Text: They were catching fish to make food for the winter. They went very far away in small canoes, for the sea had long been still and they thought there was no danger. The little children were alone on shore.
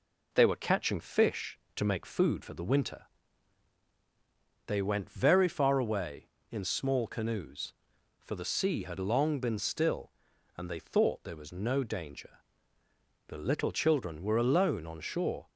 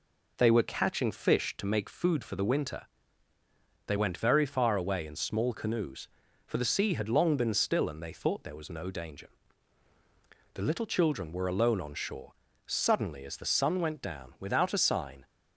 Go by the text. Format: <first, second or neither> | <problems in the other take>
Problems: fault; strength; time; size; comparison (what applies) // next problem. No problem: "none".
first | goes on to say "Suddenly as the sun went down without a sign"; strong; from 12.6 s on; 2.6 s long